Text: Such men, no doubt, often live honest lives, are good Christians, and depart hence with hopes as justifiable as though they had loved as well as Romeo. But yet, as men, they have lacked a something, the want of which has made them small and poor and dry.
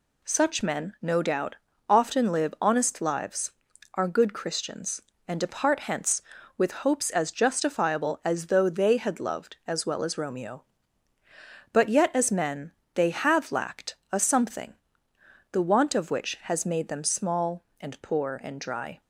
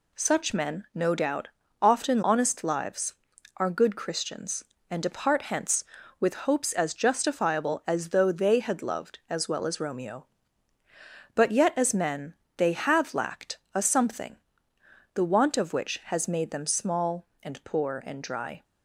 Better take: first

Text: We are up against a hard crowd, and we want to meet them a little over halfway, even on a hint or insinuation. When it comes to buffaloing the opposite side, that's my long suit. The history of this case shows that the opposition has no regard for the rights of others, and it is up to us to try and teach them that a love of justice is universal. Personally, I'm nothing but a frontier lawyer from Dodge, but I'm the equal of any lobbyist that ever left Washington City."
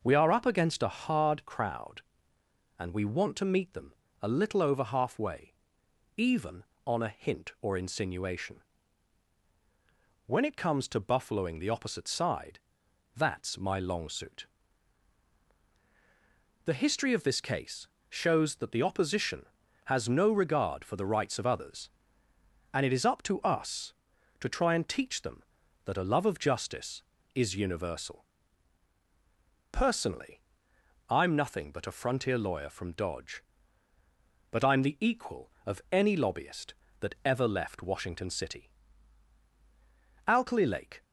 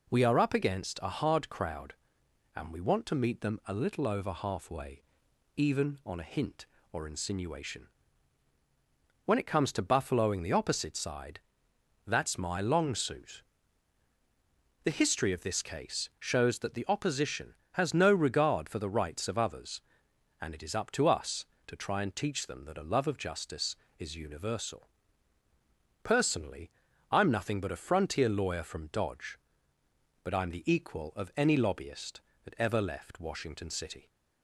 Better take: second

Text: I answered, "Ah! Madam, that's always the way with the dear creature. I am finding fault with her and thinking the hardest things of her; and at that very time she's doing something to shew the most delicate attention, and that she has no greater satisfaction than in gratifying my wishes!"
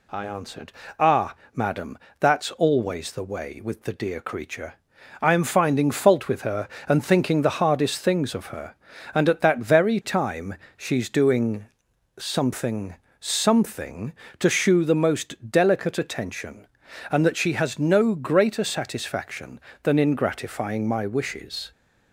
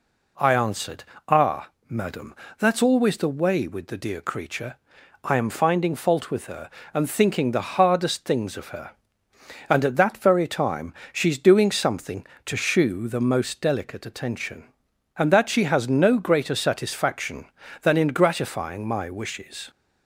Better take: second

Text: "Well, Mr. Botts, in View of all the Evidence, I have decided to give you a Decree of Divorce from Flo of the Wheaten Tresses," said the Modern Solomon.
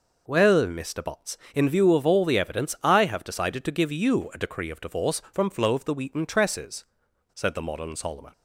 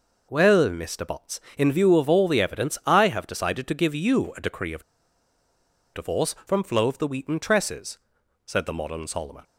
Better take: first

